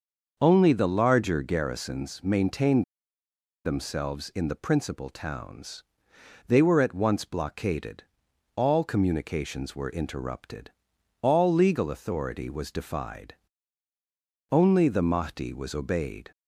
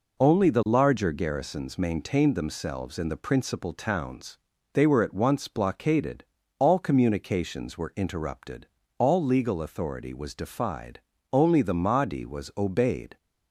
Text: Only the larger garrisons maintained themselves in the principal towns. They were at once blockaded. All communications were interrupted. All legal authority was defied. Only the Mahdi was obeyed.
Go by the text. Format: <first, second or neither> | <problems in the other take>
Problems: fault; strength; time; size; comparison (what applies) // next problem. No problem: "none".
second | starts louder than the rest; until 1.4 s; 6.5 dB // pauses between "maintained" and "themselves"; noticeable; at 2.8 s; 0.81 s long